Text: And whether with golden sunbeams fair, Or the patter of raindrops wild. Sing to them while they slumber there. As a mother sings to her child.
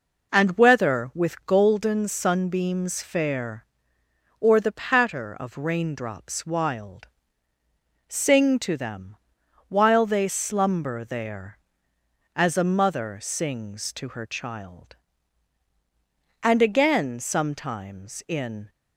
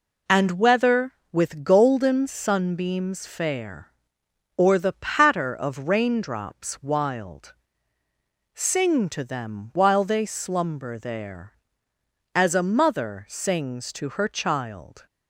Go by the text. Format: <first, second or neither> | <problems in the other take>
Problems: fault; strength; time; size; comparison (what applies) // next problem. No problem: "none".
second | pauses between "them" and "while"; noticeable; at 9.1 s; 0.52 s long // goes on to say "And again sometimes in"; strong; from 16.4 s on; 2.2 s long